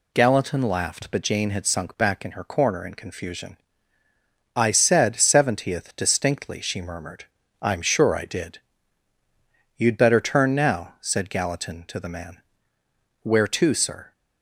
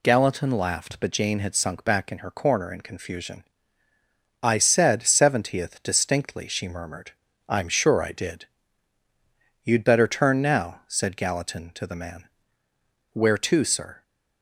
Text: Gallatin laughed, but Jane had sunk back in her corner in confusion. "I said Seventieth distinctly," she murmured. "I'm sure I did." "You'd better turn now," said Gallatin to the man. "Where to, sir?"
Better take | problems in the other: neither | none

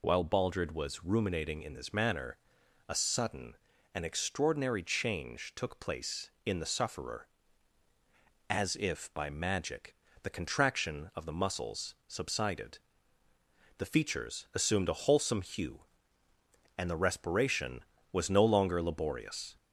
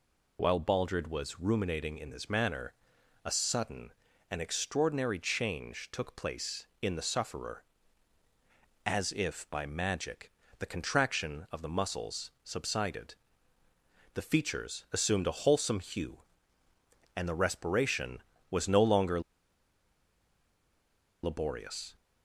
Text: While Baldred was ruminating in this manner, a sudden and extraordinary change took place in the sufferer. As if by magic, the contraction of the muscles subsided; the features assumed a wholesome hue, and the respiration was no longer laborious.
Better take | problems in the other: first | pauses between "longer" and "laborious"; strong; at 19.2 s; 2.0 s long

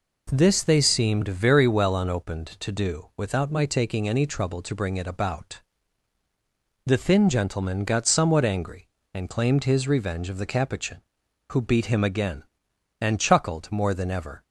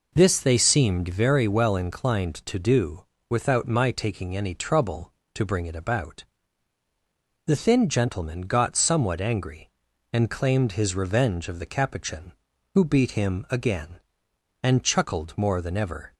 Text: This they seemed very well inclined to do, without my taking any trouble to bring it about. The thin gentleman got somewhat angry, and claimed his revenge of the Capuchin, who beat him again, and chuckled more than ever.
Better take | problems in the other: second | says "unopened" for "inclined"; at 1.9 s

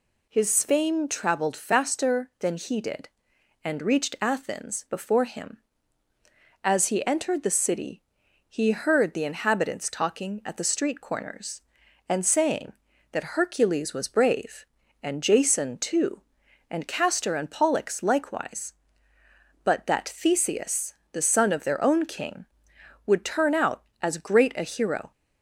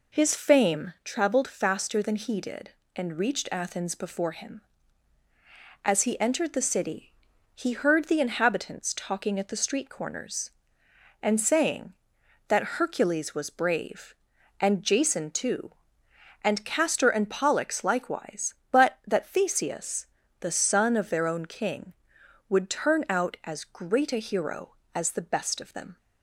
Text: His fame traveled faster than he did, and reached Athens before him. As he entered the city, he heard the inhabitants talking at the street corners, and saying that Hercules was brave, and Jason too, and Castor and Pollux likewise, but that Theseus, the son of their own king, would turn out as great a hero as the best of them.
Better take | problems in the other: second | stops before "as the best of them"; at 25.1 s

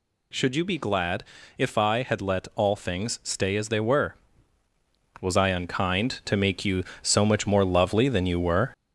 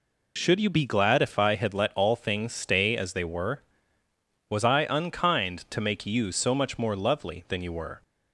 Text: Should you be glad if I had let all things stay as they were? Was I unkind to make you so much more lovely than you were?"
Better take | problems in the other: second | gets louder; noticeable; throughout; 4 dB // pauses between "glad" and "if"; slight; at 1.2 s; 0.34 s long

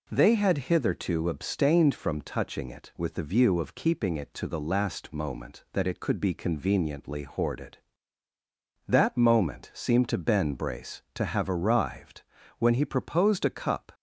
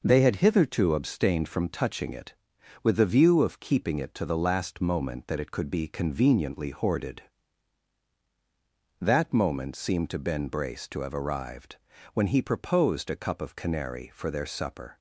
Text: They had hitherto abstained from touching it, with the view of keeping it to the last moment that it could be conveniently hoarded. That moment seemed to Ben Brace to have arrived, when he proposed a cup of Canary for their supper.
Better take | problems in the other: second | stops before "of Canary for their supper"; at 13.9 s

